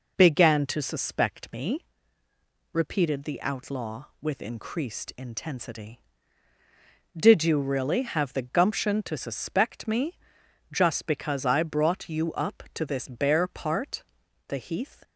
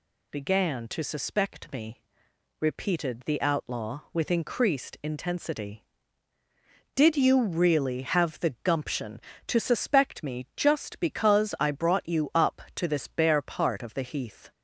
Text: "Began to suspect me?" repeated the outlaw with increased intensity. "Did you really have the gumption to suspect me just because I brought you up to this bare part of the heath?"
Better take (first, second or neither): second